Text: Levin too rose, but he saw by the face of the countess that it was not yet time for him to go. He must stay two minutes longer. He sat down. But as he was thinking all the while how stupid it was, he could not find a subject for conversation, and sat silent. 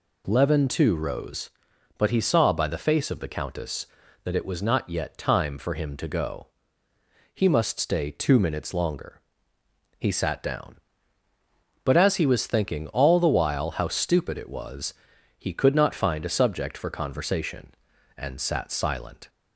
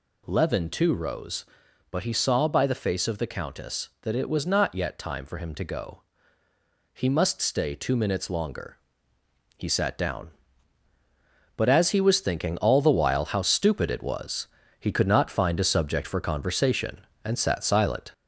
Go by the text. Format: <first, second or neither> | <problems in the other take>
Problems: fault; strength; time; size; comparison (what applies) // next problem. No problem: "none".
first | gets louder; slight; throughout; 3 dB